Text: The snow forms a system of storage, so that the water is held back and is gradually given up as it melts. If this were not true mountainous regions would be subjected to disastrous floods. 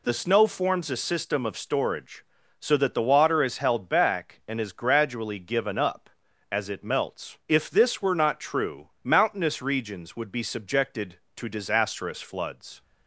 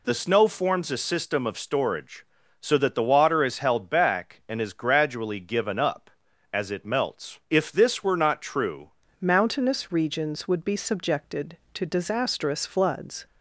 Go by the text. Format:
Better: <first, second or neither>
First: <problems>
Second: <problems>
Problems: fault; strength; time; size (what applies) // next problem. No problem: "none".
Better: first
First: none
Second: changes voice at "mountainous"; from 9.2 s on; 4.0 s long